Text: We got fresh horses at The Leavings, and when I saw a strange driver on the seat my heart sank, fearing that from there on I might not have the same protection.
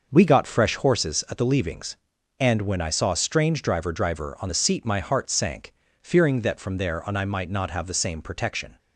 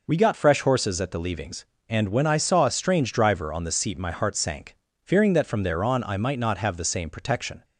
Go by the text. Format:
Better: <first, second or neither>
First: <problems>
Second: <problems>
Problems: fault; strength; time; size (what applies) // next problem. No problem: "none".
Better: second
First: starts louder than the rest; noticeable; until 1.1 s; 6 dB // says "driver" twice; at 3.9 s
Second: none